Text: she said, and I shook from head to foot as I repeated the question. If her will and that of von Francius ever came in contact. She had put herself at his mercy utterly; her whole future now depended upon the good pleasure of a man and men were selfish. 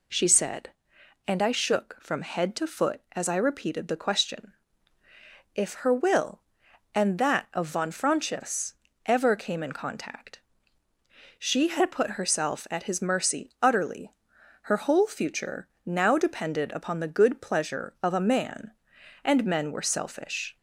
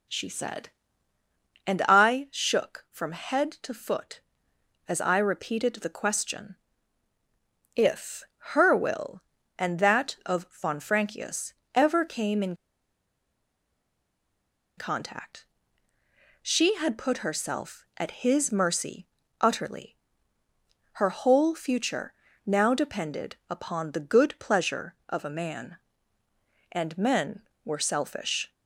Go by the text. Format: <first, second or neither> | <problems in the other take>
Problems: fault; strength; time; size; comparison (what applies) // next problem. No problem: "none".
first | pauses between "If" and "her"; slight; at 8.2 s; 0.16 s long // pauses between "Francius" and "ever"; slight; at 11.5 s; 0.22 s long; slight in the first // pauses between "in" and "contact"; strong; at 12.5 s; 2.2 s long // pauses between "mercy" and "utterly"; slight; at 19.0 s; 0.34 s long // pauses between "future" and "now"; slight; at 22.1 s; 0.32 s long; slight in the first